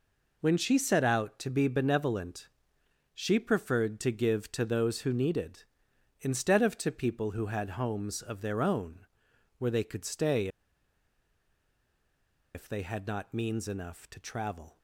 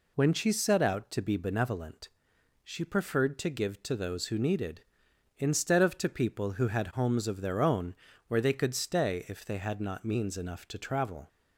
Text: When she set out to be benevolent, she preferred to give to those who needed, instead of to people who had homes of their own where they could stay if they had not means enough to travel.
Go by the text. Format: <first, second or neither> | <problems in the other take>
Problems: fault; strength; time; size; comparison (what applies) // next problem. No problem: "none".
second | pauses between "own" and "where"; noticeable; at 8.9 s; 0.58 s long; slight in the second // pauses between "stay" and "if"; strong; at 10.4 s; 2.0 s long